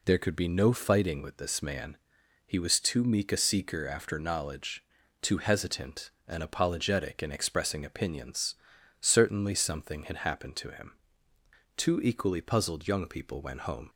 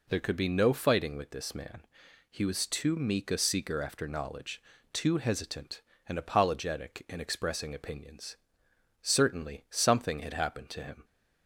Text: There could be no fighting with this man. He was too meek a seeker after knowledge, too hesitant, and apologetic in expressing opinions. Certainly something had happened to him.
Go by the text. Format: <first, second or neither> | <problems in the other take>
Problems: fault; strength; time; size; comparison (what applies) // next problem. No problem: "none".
second | goes on to say "Two equally puzzled young people went home"; strong; from 11.7 s on; 2.1 s long